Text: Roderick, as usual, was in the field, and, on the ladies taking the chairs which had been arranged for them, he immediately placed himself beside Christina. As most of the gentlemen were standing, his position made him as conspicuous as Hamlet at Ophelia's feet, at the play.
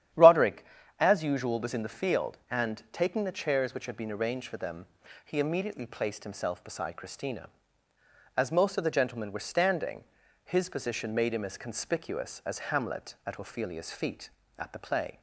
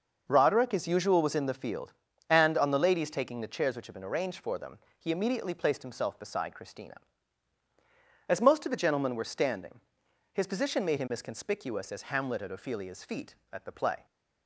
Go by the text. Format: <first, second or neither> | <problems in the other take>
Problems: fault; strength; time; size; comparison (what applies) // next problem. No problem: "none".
second | starts louder than the rest; strong; until 1.4 s; 11 dB; noticeable in the second // skips "on the ladies"; at 2.8 s